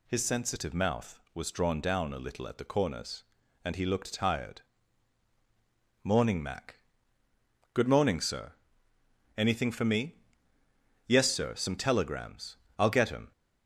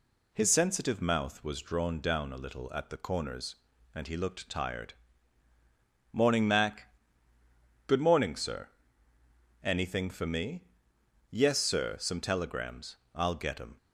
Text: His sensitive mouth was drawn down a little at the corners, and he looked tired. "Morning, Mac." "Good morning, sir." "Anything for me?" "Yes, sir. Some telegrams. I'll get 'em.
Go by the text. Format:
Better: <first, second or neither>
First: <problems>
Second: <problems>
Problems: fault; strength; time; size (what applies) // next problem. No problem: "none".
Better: neither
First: none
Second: none